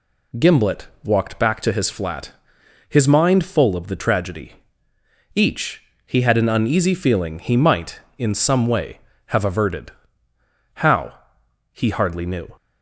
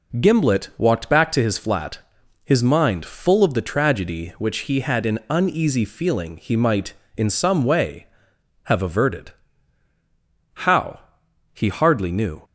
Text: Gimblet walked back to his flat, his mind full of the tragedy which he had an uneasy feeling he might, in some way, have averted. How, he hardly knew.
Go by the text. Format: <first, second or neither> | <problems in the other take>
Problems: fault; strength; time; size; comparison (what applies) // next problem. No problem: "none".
second | pauses between "Gimblet" and "walked"; slight; at 0.8 s; 0.16 s long // says "each" for "which"; at 5.3 s